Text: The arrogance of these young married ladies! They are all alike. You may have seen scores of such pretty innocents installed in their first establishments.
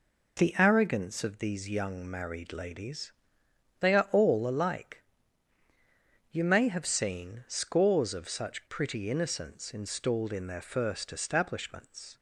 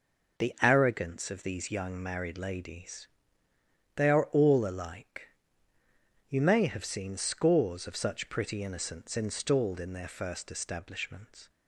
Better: neither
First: none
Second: none

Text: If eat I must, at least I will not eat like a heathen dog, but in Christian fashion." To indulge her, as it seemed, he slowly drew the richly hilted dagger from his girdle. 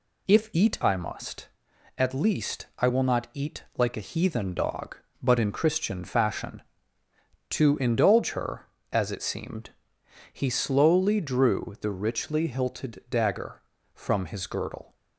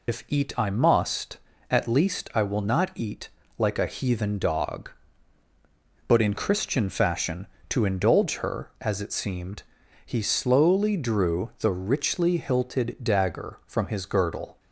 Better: first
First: none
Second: loses the start of "If"; at 0.0 s; 105 ms // pauses between "eat" and "like"; slight; at 3.2 s; 0.30 s long

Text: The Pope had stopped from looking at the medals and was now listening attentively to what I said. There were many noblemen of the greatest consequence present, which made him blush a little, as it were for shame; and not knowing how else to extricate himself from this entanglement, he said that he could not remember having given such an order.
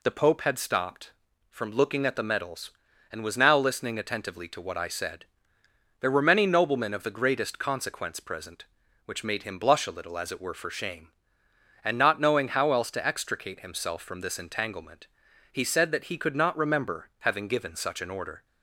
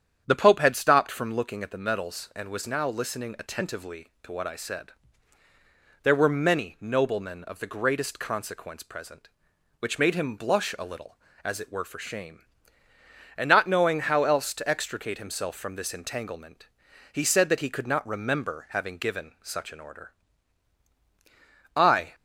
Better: first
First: none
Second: starts louder than the rest; strong; until 1.2 s; 8.5 dB // goes on to say "I"; slight; from 21.7 s on; 0.38 s long

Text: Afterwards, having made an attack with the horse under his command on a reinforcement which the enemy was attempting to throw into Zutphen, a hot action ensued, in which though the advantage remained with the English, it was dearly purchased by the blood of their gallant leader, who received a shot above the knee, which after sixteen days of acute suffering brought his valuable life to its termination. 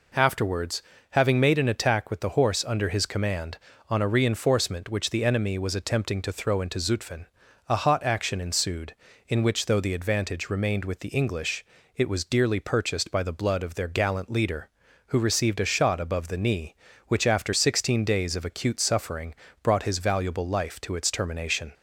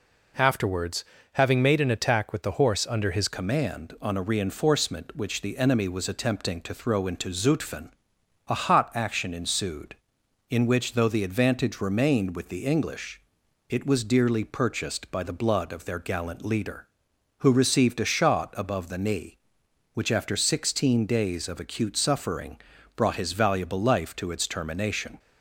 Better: first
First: pauses between "suffering" and "brought"; slight; at 19.3 s; 0.30 s long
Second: changes voice at "command"; from 3.2 s on; 21.9 s long // pauses between "suffering" and "brought"; at 22.5 s; 0.38 s long

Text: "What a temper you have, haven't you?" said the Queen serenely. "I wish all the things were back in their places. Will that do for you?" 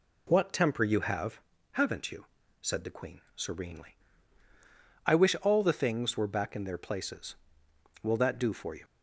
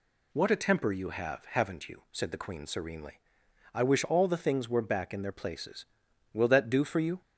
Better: second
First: skips "a"; at 0.5 s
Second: none

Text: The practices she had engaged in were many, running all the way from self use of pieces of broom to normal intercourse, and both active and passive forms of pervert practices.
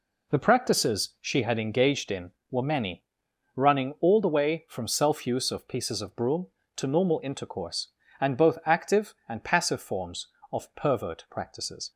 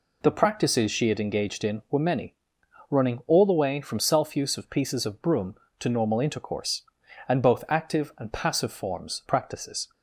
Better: first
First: none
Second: skips "of pervert"; at 9.2 s

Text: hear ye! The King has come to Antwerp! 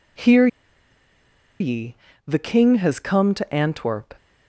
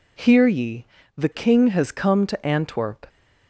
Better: second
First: pauses between "hear" and "ye"; at 0.4 s; 1.1 s long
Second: none

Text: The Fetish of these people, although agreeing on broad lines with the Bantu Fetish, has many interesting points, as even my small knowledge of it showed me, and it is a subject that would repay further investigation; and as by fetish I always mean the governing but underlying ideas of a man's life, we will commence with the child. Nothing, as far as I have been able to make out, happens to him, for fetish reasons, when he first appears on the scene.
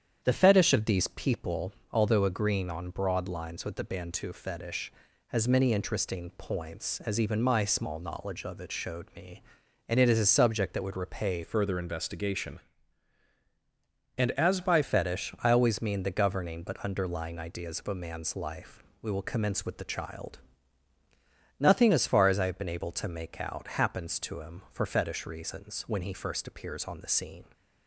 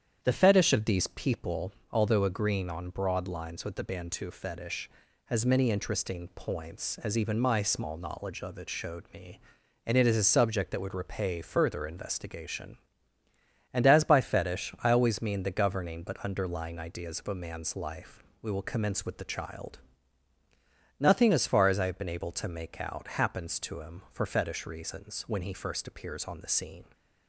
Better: second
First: starts louder than the rest; strong; until 1.2 s; 8.5 dB // changes voice from "further" to "by"; from 11.4 to 14.8 s; 3.4 s long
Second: starts louder than the rest; strong; until 1.2 s; 8.5 dB

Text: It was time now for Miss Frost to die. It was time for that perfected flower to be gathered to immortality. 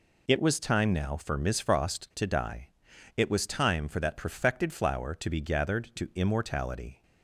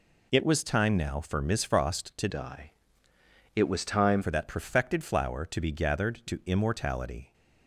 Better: first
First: none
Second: changes voice from "die" to "time"; from 2.3 to 4.2 s; 1.9 s long

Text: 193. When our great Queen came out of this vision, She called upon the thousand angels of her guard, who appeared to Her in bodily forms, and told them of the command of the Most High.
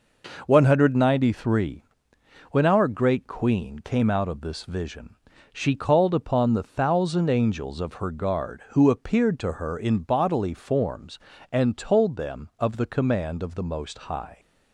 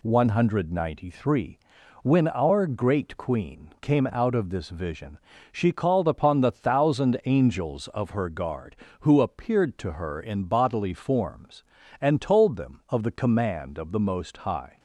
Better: neither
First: none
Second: none

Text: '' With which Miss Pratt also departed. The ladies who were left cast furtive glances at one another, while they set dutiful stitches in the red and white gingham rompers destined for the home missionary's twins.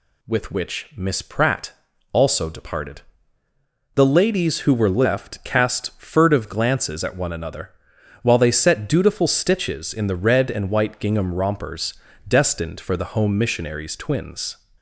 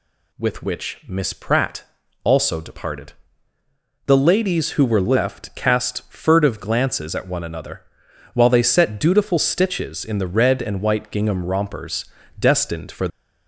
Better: first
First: pauses between "Pratt" and "also"; at 1.7 s; 0.40 s long // pauses between "rompers" and "destined"; slight; at 11.9 s; 0.32 s long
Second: pauses between "Pratt" and "also"; at 1.8 s; 0.40 s long // pauses between "rompers" and "destined"; slight; at 12.0 s; 0.32 s long // stops before "the home missionary's twins"; at 13.1 s

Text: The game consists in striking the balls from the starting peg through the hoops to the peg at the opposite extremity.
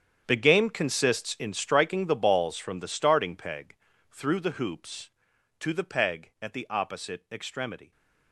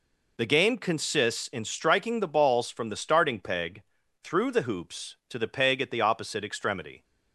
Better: second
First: gets quieter; strong; throughout; 15 dB // pauses between "peg" and "through"; slight; at 3.7 s; 0.34 s long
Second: pauses between "peg" and "through"; at 3.8 s; 0.40 s long

